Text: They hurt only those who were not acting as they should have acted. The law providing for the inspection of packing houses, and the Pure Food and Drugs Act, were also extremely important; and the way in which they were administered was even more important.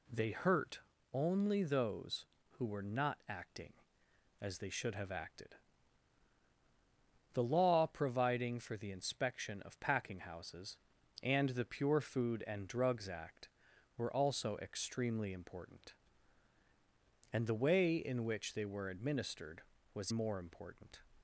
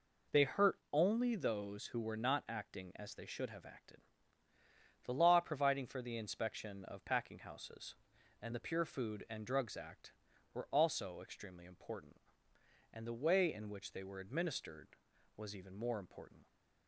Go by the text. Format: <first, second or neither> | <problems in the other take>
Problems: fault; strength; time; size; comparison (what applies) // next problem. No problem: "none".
second | pauses between "hurt" and "only"; slight; at 0.7 s; 0.34 s long // skips "even"; at 20.1 s